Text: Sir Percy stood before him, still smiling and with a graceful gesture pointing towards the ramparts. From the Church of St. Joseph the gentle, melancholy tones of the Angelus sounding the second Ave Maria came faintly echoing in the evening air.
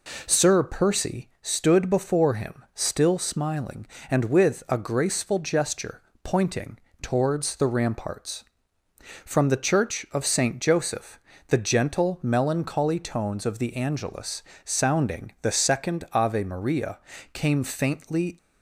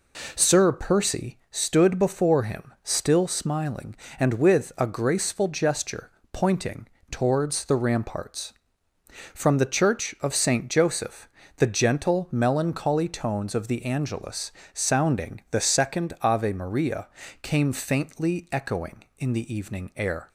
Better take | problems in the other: second | pauses between "gesture" and "pointing"; slight; at 6.0 s; 0.22 s long; slight in the second // pauses between "pointing" and "towards"; slight; at 6.7 s; 0.22 s long; slight in the second // pauses between "Joseph" and "the"; slight; at 11.1 s; 0.30 s long; slight in the second // pauses between "Angelus" and "sounding"; slight; at 14.4 s; 0.22 s long; slight in the second // pauses between "Maria" and "came"; slight; at 16.9 s; 0.32 s long; slight in the second // stops before "echoing in the evening air"; at 18.3 s

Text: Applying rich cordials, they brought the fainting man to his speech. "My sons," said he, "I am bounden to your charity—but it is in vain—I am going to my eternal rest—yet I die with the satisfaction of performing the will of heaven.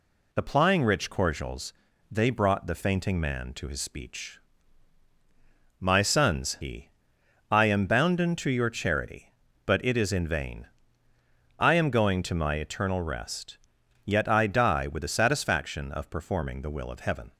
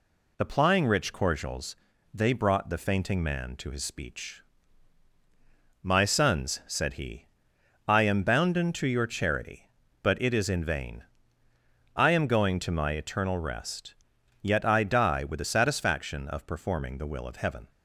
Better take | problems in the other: second | skips "said"; at 6.5 s

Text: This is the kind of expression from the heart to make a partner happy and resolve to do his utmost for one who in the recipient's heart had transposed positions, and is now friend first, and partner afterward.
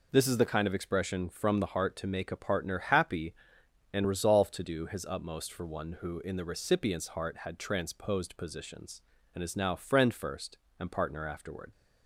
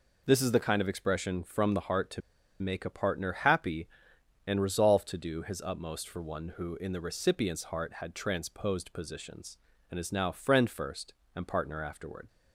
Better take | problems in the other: first | pauses between "to" and "make"; at 2.2 s; 0.40 s long

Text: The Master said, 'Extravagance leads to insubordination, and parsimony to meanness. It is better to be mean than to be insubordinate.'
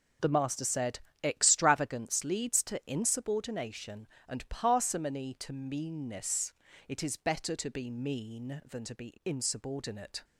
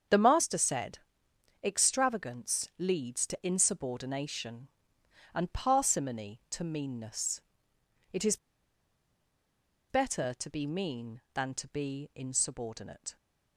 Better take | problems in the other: first | starts louder than the rest; strong; until 1.7 s; 7.5 dB // pauses between "is" and "better"; strong; at 8.3 s; 1.5 s long

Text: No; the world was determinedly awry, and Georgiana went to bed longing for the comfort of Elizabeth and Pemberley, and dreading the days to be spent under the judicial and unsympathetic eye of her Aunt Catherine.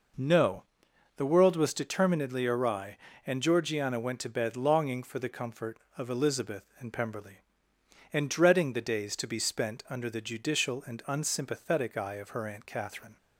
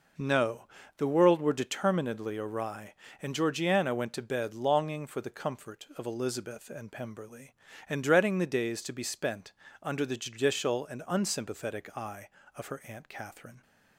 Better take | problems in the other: first | says "were" for "was"; at 1.3 s // pauses between "spent" and "under"; slight; at 9.5 s; 0.28 s long

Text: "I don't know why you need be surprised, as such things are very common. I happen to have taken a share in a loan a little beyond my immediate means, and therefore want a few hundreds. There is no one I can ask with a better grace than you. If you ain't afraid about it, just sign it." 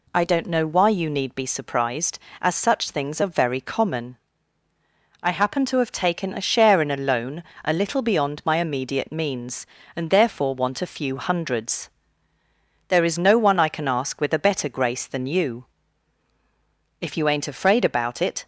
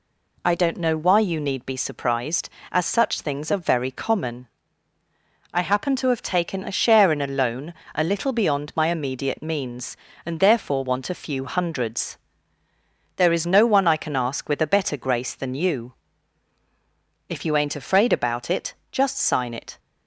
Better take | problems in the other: second | pauses between "loan" and "a"; slight; at 7.4 s; 0.22 s long; slight in the second // stops before "just sign it"; at 18.4 s

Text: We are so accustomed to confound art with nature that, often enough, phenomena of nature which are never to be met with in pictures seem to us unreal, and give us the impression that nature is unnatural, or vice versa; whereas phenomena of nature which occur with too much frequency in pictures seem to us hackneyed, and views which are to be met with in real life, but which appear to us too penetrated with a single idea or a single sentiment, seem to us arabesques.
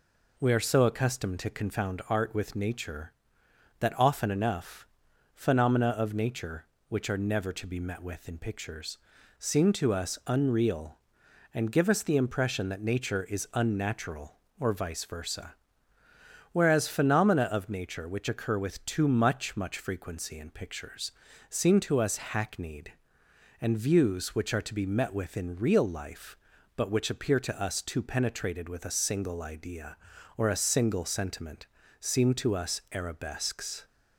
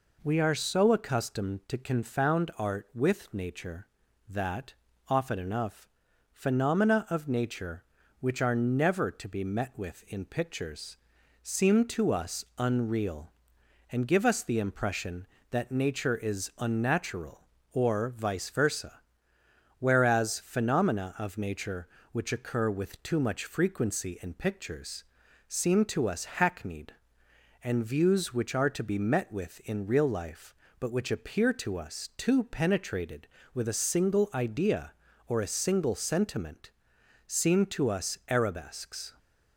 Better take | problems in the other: second | pauses between "pictures" and "seem"; at 8.9 s; 0.40 s long; noticeable in the second // says "much" twice; at 19.5 s // pauses between "pictures" and "seem"; slight; at 21.1 s; 0.36 s long; also in the second

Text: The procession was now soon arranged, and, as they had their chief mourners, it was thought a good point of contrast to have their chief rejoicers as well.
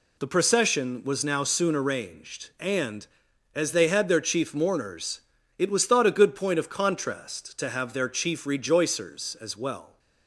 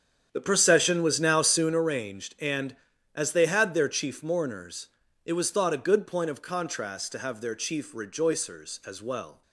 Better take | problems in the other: first | starts louder than the rest; strong; until 1.9 s; 8 dB

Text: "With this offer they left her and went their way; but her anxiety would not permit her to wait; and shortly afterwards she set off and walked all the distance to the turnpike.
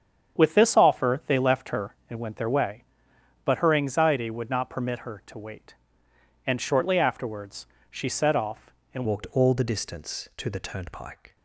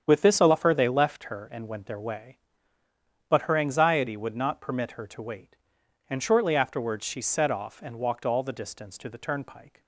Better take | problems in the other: second | starts louder than the rest; strong; until 1.3 s; 8 dB; strong in the second // pauses between "afterwards" and "she"; slight; at 7.6 s; 0.24 s long // changes voice at "walked"; from 9.0 s on; 2.3 s long

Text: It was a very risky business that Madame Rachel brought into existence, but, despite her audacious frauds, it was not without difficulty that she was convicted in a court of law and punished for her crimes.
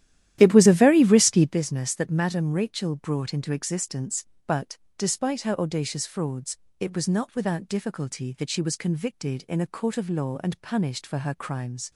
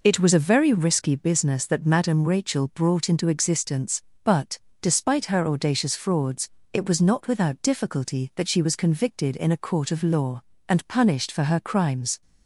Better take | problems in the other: second | starts louder than the rest; strong; until 1.6 s; 12 dB

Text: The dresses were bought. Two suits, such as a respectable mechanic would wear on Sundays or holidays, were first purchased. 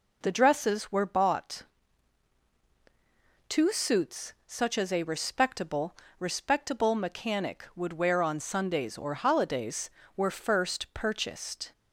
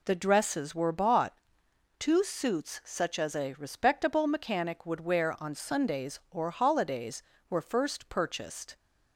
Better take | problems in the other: second | says "respectable" twice; at 6.1 s

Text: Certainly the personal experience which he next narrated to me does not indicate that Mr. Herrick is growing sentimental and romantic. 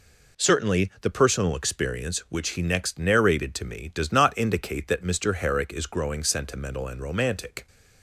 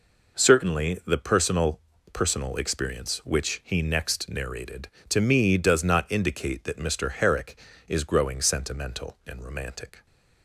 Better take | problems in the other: first | says "personal" twice; at 2.1 s

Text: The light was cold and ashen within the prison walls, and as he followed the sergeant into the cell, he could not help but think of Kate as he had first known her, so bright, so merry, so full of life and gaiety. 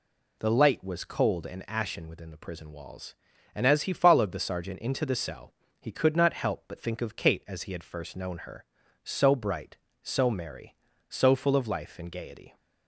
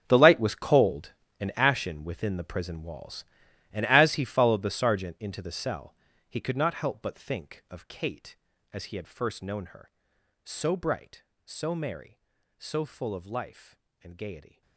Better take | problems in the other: first | gets quieter; strong; throughout; 15.5 dB

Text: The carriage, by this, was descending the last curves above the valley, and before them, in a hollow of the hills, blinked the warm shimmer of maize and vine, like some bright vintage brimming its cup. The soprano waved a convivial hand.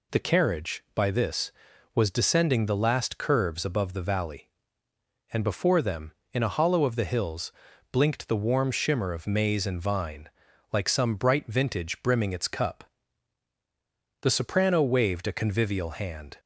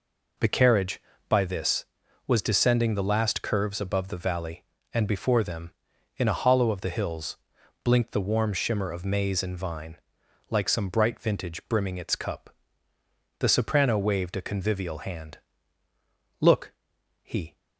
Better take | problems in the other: first | goes on to say "Look he"; noticeable; from 16.3 s on; 1.1 s long

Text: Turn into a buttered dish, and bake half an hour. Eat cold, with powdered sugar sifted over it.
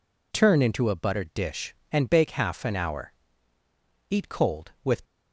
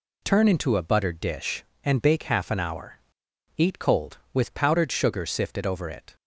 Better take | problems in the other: second | stops before "powdered sugar sifted over it"; at 5.0 s

